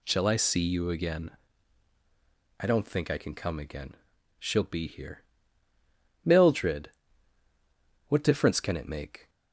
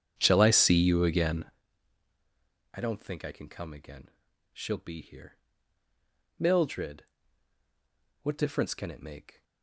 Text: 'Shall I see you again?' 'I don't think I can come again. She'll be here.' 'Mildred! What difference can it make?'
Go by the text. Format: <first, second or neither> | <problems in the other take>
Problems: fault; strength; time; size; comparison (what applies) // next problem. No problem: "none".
first | starts louder than the rest; strong; until 1.6 s; 8.5 dB